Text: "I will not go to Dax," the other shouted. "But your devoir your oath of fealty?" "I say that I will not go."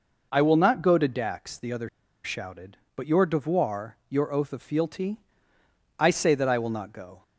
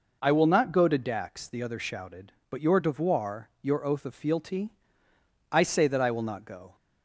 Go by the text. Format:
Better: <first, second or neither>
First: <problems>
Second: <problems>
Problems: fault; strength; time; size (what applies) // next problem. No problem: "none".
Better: second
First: pauses between "other" and "shouted"; at 1.8 s; 0.36 s long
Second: none